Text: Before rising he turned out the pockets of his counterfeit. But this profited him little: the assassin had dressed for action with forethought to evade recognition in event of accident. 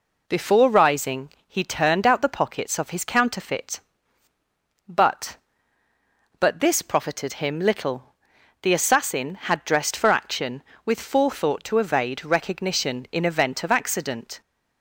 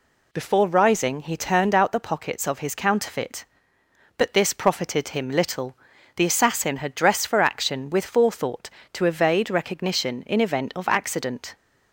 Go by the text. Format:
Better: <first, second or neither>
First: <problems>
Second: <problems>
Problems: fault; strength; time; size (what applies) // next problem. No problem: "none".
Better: second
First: pauses between "rising" and "he"; slight; at 1.3 s; 0.16 s long // says "But" twice; at 6.4 s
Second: none